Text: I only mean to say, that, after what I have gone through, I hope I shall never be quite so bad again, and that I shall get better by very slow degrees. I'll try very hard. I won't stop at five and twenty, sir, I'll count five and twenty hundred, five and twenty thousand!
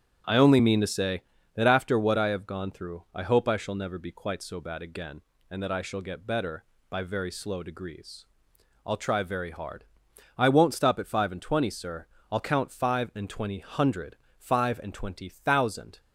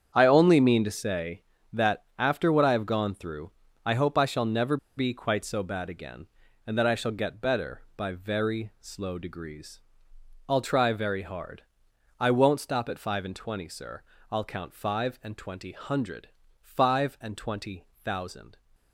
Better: first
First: starts louder than the rest; strong; until 1.5 s; 9 dB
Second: starts louder than the rest; strong; until 1.1 s; 8 dB // pauses between "never" and "be"; slight; at 4.7 s; 0.19 s long

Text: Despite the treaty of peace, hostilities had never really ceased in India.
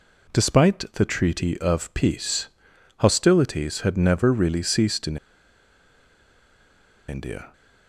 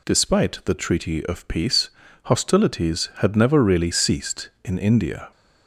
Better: second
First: pauses between "in" and "India"; strong; at 5.1 s; 1.9 s long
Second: none

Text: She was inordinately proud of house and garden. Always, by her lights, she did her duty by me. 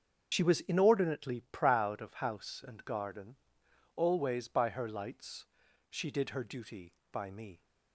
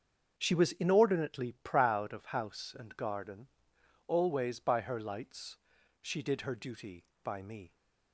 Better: second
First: loses the start of "She"; at 0.3 s; 50 ms // starts louder than the rest; until 1.3 s; 7 dB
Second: starts louder than the rest; until 1.3 s; 6.5 dB

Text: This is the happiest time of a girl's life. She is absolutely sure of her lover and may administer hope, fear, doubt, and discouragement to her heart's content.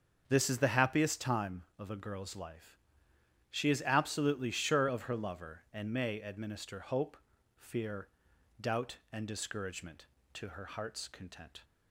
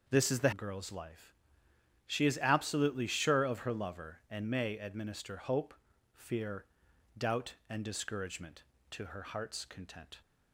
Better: first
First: starts louder than the rest; until 1.2 s; 7 dB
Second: starts louder than the rest; noticeable; until 1.1 s; 6 dB // skips "happiest time of a"; at 0.5 s

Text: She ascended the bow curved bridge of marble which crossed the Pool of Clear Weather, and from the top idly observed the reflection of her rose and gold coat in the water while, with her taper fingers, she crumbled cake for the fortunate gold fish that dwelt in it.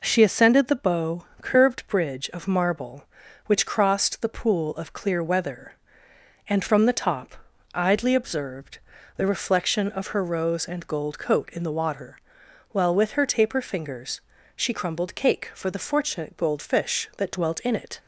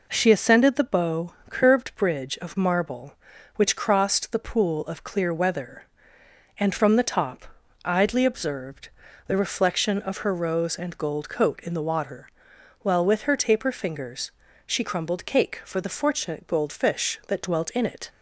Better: neither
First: pauses between "bow" and "curved"; slight; at 1.2 s; 0.18 s long // pauses between "top" and "idly"; at 7.3 s; 0.38 s long // pauses between "observed" and "the"; at 8.7 s; 0.40 s long // pauses between "water" and "while"; noticeable; at 12.1 s; 0.54 s long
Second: pauses between "bow" and "curved"; slight; at 1.3 s; 0.18 s long // pauses between "top" and "idly"; at 7.4 s; 0.38 s long // pauses between "observed" and "the"; at 8.8 s; 0.40 s long // pauses between "water" and "while"; noticeable; at 12.2 s; 0.54 s long

